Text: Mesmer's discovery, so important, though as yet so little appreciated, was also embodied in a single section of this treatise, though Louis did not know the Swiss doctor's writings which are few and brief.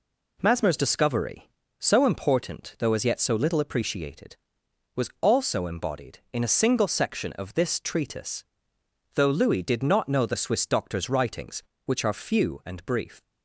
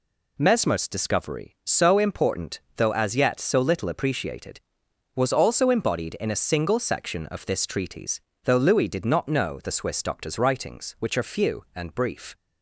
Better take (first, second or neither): neither